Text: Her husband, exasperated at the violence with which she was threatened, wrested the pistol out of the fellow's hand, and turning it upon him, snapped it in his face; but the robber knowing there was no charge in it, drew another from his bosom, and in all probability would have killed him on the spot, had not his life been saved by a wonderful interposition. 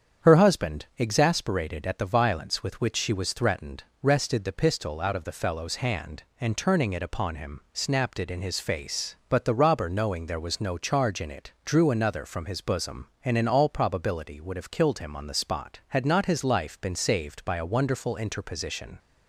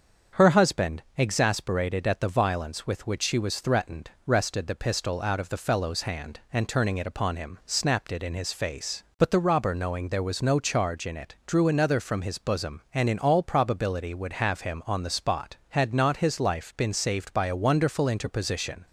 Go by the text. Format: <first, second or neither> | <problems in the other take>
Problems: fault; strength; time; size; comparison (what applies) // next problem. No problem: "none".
first | starts louder than the rest; strong; until 1.4 s; 7 dB; strong in the first // skips "killed"; at 14.6 s